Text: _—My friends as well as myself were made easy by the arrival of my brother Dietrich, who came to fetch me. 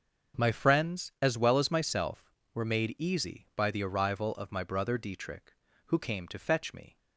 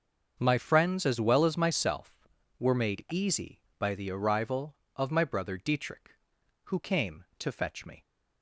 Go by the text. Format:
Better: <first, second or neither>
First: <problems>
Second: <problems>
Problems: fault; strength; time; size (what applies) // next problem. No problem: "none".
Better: neither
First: starts louder than the rest; until 1.4 s; 6.5 dB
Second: starts louder than the rest; until 1.4 s; 6.5 dB